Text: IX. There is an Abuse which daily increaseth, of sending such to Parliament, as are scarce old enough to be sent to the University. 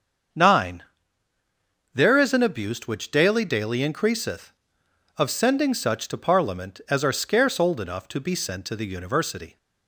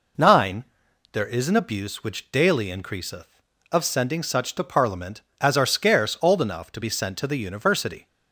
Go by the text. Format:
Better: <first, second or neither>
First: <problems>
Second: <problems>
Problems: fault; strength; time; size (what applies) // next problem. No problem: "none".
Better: second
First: starts louder than the rest; until 2.4 s; 7 dB // says "daily" twice; at 3.4 s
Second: none